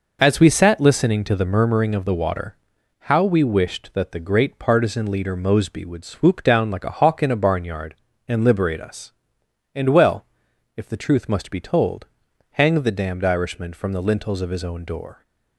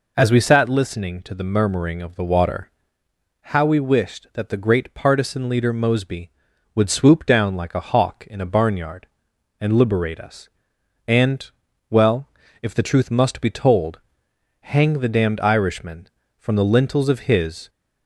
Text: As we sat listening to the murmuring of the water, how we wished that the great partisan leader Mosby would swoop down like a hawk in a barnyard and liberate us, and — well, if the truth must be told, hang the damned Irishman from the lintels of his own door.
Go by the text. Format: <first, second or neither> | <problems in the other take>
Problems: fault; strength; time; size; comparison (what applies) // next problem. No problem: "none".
first | stops before "own door"; at 17.6 s